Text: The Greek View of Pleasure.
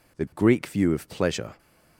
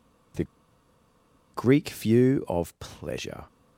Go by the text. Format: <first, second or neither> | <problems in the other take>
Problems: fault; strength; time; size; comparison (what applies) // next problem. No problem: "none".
first | pauses between "The" and "Greek"; at 0.4 s; 1.0 s long